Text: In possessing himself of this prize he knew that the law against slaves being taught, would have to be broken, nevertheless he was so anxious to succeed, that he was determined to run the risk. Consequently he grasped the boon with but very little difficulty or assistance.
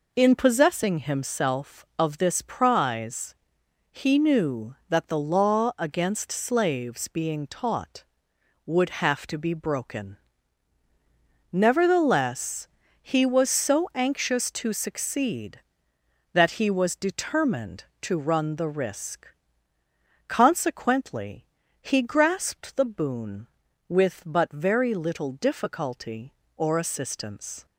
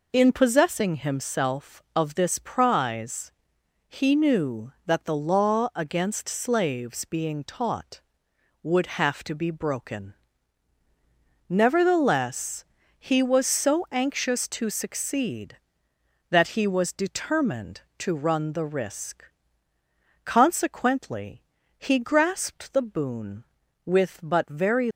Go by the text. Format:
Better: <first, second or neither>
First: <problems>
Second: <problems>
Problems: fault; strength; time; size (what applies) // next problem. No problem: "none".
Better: first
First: pauses between "prize" and "he"; noticeable; at 3.3 s; 0.58 s long // pauses between "nevertheless" and "he"; slight; at 12.6 s; 0.34 s long // pauses between "Consequently" and "he"; slight; at 21.4 s; 0.34 s long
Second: pauses between "prize" and "he"; noticeable; at 3.2 s; 0.58 s long // pauses between "nevertheless" and "he"; slight; at 12.6 s; 0.34 s long // pauses between "Consequently" and "he"; slight; at 21.4 s; 0.34 s long // stops before "little difficulty or assistance"; at 24.8 s